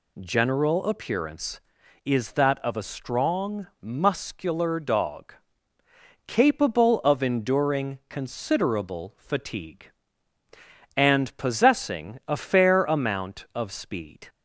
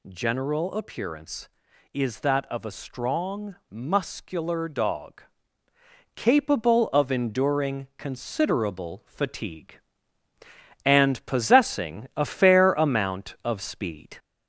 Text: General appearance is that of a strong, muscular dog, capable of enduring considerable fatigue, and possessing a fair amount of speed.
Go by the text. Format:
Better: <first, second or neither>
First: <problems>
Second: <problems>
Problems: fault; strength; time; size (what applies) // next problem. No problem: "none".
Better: first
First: none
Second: gets louder; slight; throughout; 2.5 dB